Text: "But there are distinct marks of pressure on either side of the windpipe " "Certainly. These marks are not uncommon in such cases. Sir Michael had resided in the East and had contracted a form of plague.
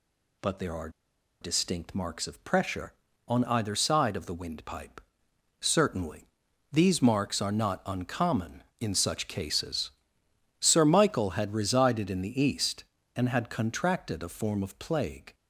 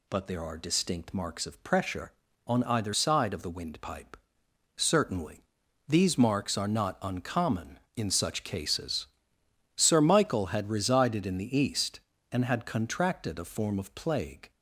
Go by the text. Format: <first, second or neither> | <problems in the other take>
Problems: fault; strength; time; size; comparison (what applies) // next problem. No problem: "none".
second | pauses between "are" and "distinct"; noticeable; at 0.8 s; 0.52 s long